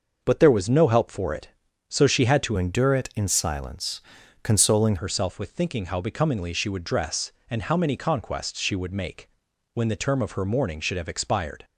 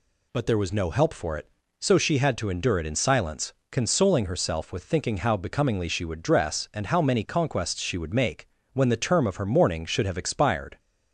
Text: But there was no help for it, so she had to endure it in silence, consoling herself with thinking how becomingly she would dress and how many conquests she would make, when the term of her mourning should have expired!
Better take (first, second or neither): second